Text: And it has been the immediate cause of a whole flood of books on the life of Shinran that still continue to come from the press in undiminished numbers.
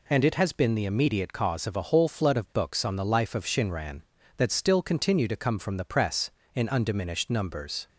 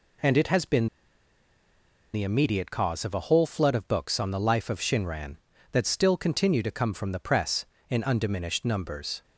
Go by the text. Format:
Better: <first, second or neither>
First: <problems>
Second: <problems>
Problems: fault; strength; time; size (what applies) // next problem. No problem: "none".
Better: first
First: none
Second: pauses between "been" and "the"; strong; at 0.8 s; 1.2 s long